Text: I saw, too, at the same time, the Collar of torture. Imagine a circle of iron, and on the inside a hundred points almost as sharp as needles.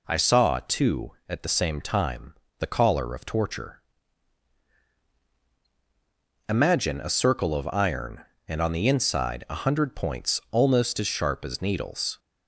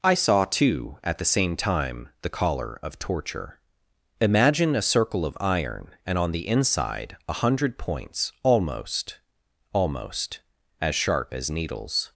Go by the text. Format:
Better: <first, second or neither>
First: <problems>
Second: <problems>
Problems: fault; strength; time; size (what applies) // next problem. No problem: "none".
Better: first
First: none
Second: says "almost" twice; at 9.7 s